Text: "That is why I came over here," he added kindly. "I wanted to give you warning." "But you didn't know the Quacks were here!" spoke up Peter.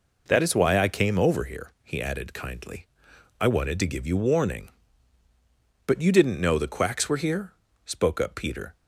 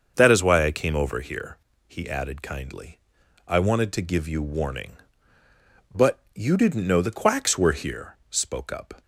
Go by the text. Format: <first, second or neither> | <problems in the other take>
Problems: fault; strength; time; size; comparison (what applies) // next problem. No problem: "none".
first | starts louder than the rest; until 1.1 s; 6.5 dB // pauses between "But" and "you"; slight; at 6.2 s; 0.16 s long // stops before "Peter"; at 9.0 s